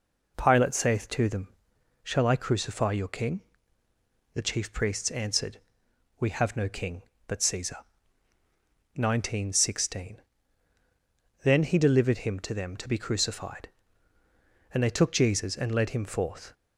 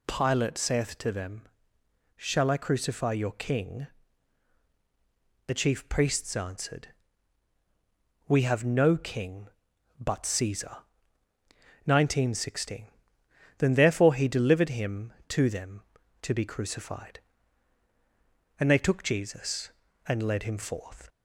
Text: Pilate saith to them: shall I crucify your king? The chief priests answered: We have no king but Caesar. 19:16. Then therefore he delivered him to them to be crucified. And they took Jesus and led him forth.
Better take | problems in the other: second | skips "therefore"; at 11.6 s

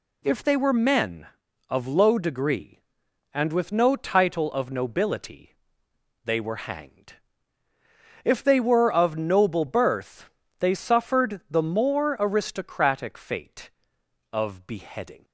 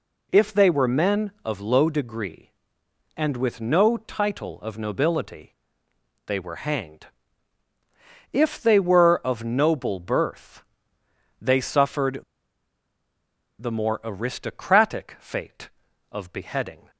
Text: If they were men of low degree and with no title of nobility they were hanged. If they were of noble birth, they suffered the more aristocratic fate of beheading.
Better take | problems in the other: first | pauses between "nobility" and "they"; noticeable; at 5.5 s; 0.72 s long; noticeable in the first // pauses between "suffered" and "the"; strong; at 12.2 s; 1.3 s long

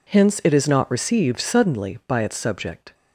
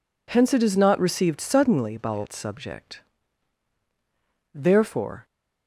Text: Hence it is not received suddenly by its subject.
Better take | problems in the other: first | goes on to say "Therefore"; noticeable; from 4.5 s on; 0.72 s long

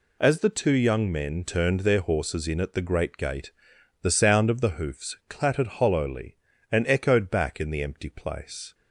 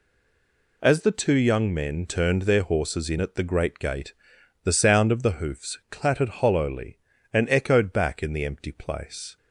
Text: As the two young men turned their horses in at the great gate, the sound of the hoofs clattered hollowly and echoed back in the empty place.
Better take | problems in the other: first | stays silent before the first word; slight; until 0.8 s; 0.8 s long

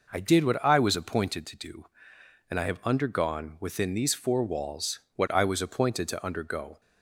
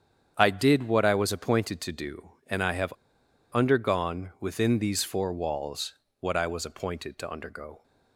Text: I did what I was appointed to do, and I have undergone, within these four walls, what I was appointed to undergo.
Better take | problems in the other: first | starts louder than the rest; strong; until 1.3 s; 8.5 dB // pauses between "have" and "undergone"; noticeable; at 2.9 s; 0.60 s long

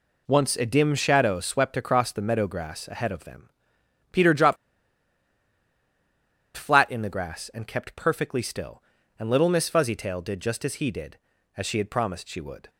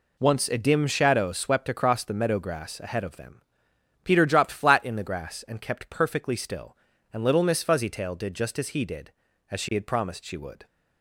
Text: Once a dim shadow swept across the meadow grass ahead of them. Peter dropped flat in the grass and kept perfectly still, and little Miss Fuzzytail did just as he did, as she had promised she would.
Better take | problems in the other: second | pauses between "dropped" and "flat"; strong; at 4.5 s; 2.0 s long

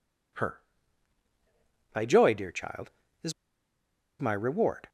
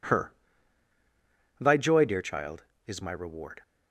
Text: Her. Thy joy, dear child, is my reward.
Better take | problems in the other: second | pauses between "is" and "my"; noticeable; at 3.3 s; 0.89 s long

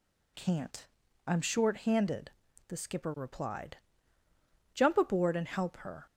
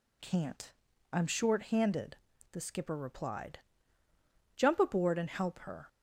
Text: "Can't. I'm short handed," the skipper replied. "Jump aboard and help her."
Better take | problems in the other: neither | none

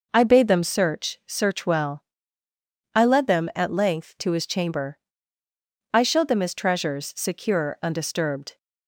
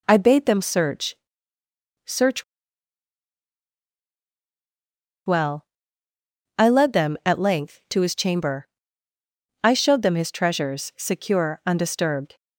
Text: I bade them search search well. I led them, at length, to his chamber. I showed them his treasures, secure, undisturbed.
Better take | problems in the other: first | pauses between "search" and "search"; noticeable; at 1.1 s; 0.90 s long // pauses between "search" and "well"; strong; at 2.4 s; 2.8 s long

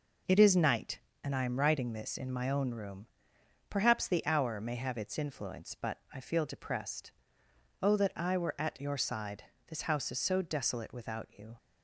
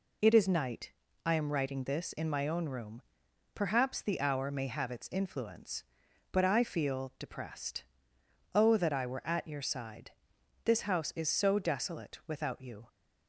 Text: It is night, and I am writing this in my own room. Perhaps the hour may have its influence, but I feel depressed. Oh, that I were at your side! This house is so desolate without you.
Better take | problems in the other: first | skips "and"; at 1.0 s

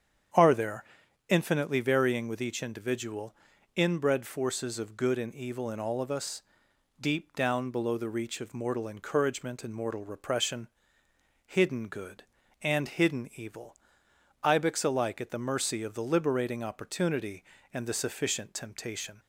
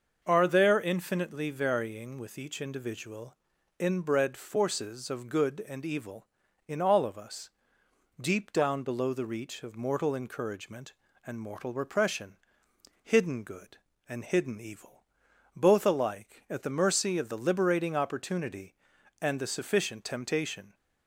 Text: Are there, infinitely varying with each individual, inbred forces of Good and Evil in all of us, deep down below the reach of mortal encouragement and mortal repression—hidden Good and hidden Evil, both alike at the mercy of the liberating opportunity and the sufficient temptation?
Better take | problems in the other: second | starts louder than the rest; strong; until 1.7 s; 8.5 dB; also in the second // says "ibex" for "both"; at 14.4 s

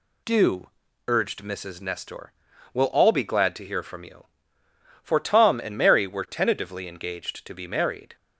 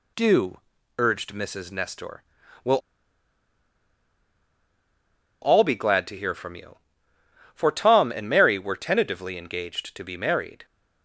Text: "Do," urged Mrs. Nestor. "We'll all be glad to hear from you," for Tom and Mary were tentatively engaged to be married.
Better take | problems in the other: first | pauses between "We'll" and "all"; strong; at 2.7 s; 2.6 s long

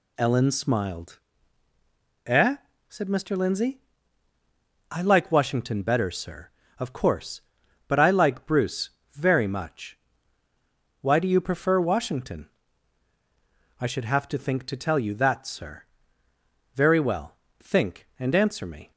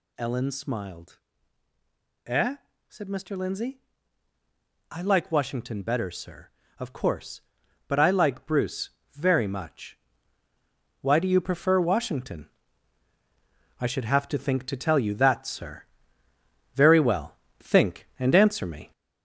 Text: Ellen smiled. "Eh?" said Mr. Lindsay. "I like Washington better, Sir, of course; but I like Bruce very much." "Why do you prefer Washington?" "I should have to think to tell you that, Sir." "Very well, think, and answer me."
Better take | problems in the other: first | gets louder; noticeable; throughout; 4.5 dB // pauses between "Bruce" and "very"; slight; at 8.8 s; 0.24 s long; slight in the first

